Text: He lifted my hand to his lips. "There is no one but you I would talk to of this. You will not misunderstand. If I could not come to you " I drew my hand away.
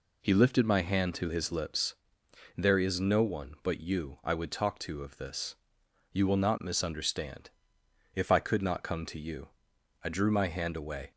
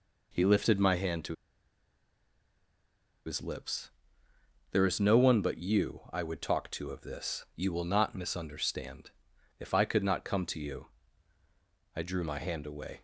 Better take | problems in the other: first | pauses between "to" and "his"; strong; at 1.3 s; 1.9 s long

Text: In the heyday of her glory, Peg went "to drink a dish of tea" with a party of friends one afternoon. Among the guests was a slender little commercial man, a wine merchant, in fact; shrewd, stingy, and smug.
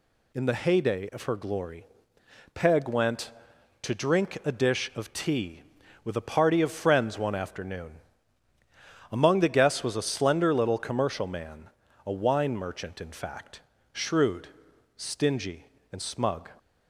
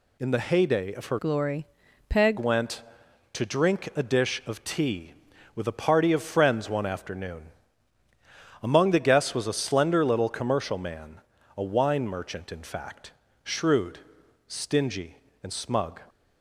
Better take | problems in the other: first | changes voice from "glory" to "Peg"; from 1.1 to 2.3 s; 1.2 s long

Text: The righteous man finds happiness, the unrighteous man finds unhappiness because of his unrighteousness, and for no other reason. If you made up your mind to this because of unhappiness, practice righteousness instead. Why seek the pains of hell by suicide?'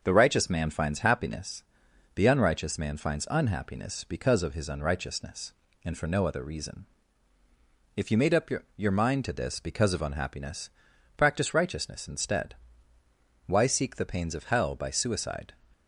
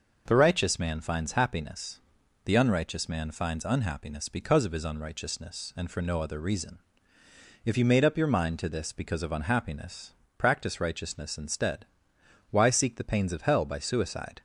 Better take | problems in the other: second | starts louder than the rest; noticeable; until 1.0 s; 6 dB // says "your" twice; at 8.7 s

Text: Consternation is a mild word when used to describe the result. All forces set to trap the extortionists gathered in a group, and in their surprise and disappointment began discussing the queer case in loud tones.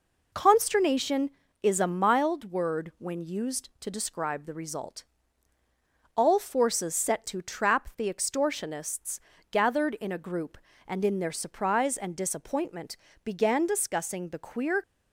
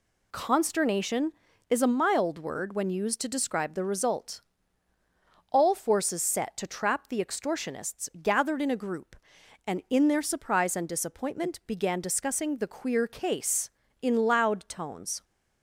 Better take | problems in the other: second | pauses between "extortionists" and "gathered"; slight; at 9.1 s; 0.30 s long // pauses between "disappointment" and "began"; slight; at 12.9 s; 0.26 s long // stops before "case in loud tones"; at 14.8 s

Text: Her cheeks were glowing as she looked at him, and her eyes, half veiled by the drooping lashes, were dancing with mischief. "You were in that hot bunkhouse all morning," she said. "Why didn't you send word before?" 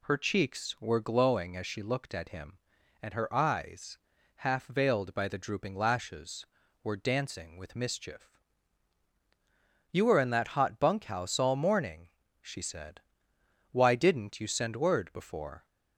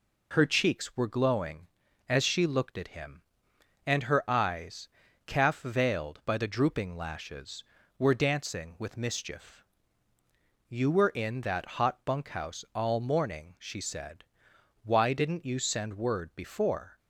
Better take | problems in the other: first | says "calf" for "half"; at 5.2 s

